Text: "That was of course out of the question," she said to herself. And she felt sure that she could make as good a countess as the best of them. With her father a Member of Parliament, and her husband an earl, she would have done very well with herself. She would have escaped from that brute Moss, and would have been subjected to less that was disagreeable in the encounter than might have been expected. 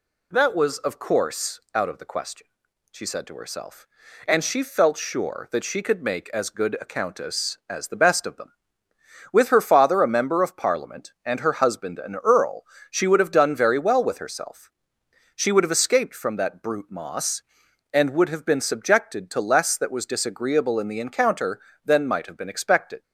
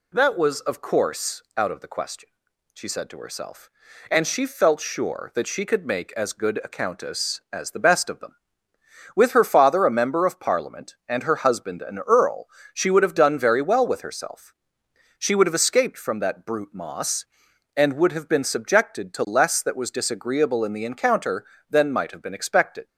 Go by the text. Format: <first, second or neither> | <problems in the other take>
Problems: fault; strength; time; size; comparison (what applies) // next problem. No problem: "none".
neither | pauses between "course" and "out"; slight; the same in both